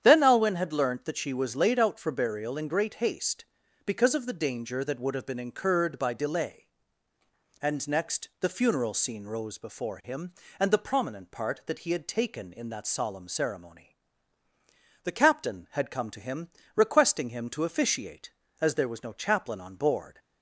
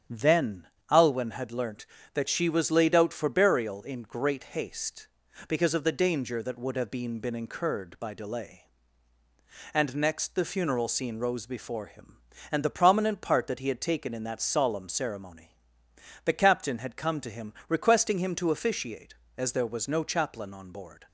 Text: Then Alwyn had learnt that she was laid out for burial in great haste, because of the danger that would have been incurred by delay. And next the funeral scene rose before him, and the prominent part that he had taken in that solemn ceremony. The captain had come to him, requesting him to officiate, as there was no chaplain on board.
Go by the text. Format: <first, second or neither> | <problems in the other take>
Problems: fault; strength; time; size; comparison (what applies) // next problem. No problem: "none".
first | starts louder than the rest; strong; until 1.3 s; 8.5 dB; strong in the first // pauses between "Then" and "Alwyn"; slight; at 0.6 s; 0.23 s long // says "been" twice; at 7.2 s